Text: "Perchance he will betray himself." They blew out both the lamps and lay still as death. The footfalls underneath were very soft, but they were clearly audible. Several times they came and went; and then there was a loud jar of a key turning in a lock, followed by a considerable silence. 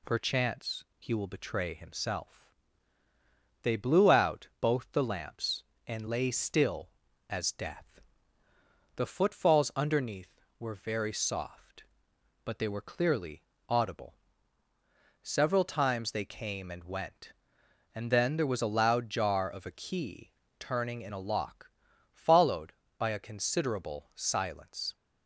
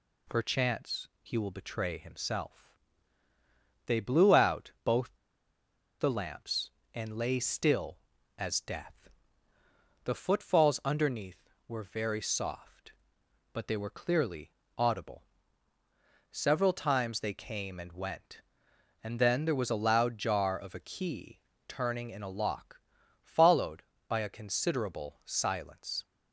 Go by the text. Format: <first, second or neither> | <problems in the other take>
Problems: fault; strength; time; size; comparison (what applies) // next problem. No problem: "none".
first | pauses between "both" and "the"; noticeable; at 5.1 s; 0.84 s long // pauses between "clearly" and "audible"; slight; at 14.5 s; 0.26 s long; slight in the first // pauses between "key" and "turning"; slight; at 21.4 s; 0.26 s long; slight in the first